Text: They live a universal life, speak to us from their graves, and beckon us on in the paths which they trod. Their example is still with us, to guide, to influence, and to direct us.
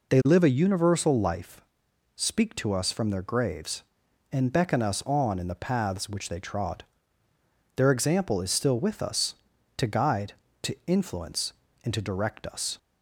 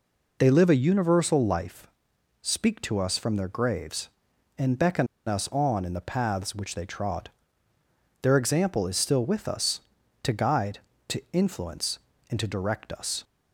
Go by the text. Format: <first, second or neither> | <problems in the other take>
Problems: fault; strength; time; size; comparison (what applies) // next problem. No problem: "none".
first | pauses between "beckon" and "us"; slight; at 5.0 s; 0.20 s long